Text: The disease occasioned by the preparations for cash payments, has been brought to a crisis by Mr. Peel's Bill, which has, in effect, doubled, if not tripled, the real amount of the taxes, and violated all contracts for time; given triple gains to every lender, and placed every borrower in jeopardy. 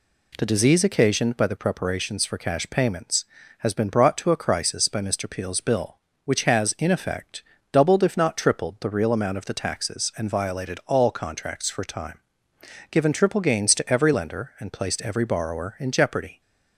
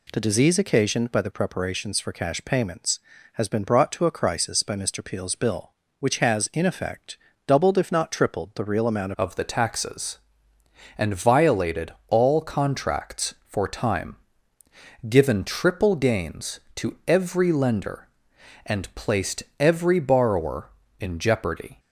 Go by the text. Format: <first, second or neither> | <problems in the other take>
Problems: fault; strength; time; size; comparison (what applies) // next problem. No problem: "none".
first | changes voice at "of"; from 9.1 s on; 12.6 s long // pauses between "violated" and "all"; slight; at 11.9 s; 0.16 s long // pauses between "placed" and "every"; slight; at 19.4 s; 0.16 s long